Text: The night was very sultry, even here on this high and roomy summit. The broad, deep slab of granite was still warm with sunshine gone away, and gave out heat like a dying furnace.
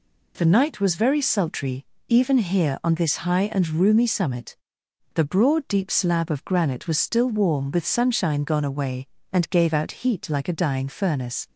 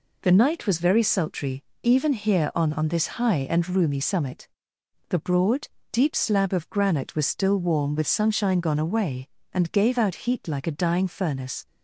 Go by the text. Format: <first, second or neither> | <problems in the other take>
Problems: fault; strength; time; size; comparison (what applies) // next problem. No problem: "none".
first | says "on" twice; at 2.7 s